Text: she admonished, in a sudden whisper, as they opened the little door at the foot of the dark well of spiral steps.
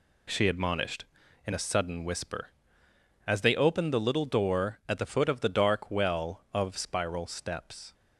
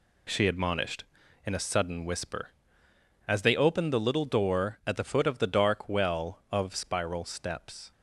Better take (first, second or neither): neither